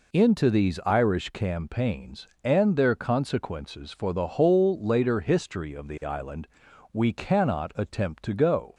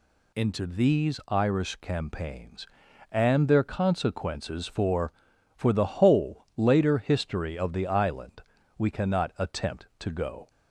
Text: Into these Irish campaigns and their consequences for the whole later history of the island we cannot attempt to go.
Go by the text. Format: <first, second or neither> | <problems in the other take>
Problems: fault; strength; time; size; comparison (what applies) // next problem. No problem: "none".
first | says "for" twice; at 5.5 s // pauses between "island" and "we"; at 8.4 s; 0.38 s long; also in the first